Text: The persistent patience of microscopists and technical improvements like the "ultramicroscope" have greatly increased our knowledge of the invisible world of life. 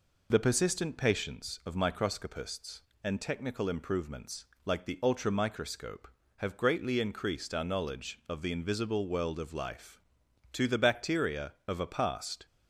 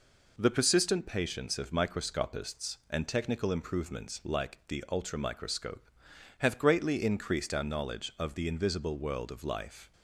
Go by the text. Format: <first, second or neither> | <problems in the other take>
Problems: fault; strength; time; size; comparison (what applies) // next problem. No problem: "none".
second | pauses between "improvements" and "like"; slight; at 4.4 s; 0.18 s long // goes on to say "To the bacteria of a past"; strong; from 10.5 s on; 1.9 s long